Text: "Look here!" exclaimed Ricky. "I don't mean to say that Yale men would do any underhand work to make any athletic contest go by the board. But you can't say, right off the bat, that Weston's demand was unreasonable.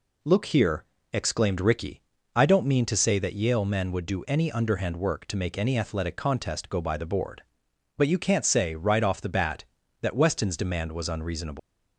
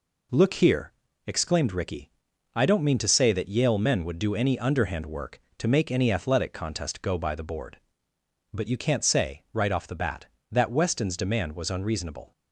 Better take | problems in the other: second | leaves "unreasonable" unfinished; at 11.5 s; 155 ms

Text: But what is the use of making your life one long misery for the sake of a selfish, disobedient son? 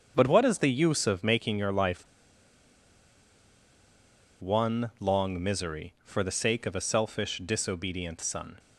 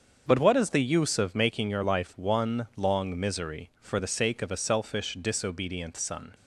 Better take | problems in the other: second | starts louder than the rest; until 1.1 s; 7 dB; also in the second // pauses between "life" and "one"; strong; at 2.0 s; 2.3 s long

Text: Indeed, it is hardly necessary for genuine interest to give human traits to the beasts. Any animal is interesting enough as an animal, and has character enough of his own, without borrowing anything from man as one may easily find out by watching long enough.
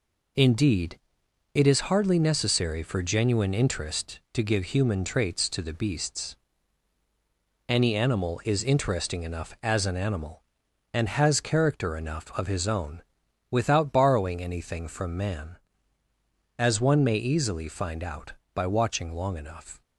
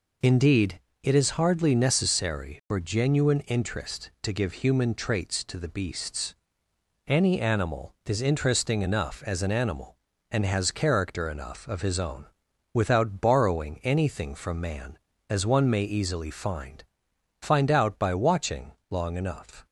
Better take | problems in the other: first | says "find" twice; at 17.3 s // pauses between "watching" and "long"; slight; at 18.7 s; 0.18 s long

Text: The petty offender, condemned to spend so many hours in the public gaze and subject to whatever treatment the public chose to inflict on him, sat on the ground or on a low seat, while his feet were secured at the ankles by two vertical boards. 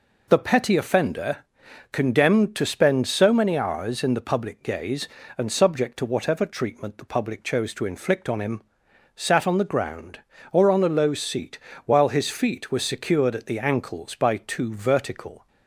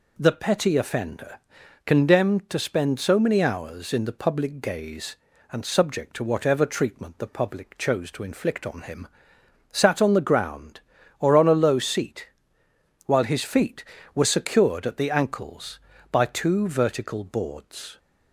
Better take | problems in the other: second | stops before "boards"; at 15.4 s

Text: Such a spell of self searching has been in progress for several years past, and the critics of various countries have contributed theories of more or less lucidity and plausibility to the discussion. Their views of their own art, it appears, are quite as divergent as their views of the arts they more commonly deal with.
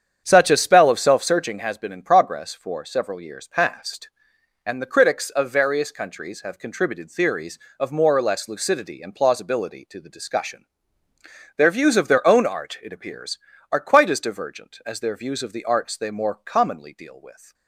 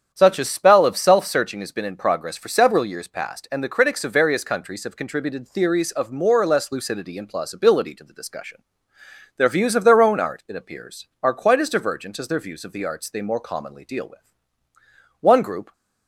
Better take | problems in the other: first | starts louder than the rest; strong; until 1.1 s; 8 dB; strong in the first // goes on to say "One group"; from 15.2 s on; 0.52 s long

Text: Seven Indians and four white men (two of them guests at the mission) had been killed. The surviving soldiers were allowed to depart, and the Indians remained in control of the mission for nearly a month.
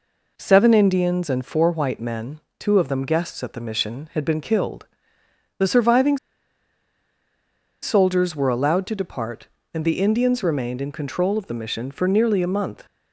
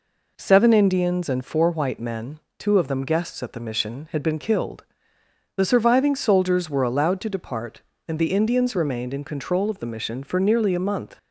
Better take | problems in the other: second | pauses between "surviving" and "soldiers"; strong; at 6.1 s; 1.6 s long

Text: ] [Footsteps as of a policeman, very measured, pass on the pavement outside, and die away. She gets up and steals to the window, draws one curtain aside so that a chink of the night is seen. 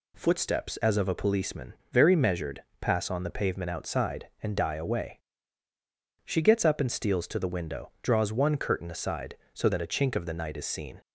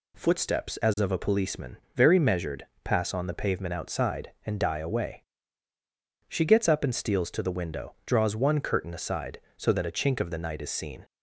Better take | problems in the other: neither | none

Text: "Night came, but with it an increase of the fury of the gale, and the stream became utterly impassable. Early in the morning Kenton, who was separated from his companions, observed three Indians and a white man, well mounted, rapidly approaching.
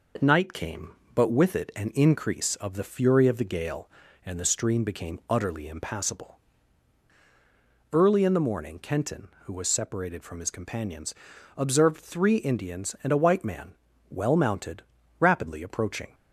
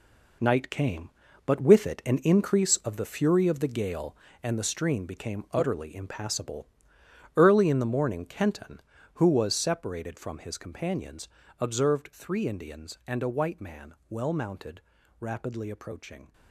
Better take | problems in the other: first | gets quieter; strong; throughout; 10 dB

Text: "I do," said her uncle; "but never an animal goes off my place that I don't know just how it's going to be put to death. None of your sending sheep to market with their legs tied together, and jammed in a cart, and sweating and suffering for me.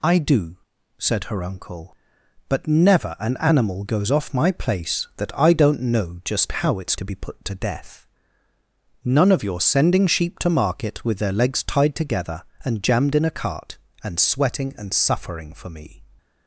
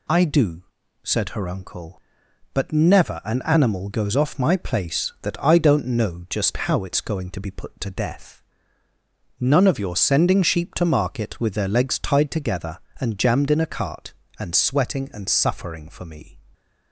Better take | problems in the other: second | skips "going"; at 6.9 s

